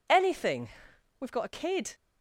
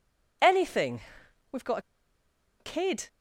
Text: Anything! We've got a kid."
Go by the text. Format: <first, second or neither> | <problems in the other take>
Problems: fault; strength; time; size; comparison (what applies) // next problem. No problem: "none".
first | pauses between "got" and "a"; noticeable; at 1.7 s; 0.80 s long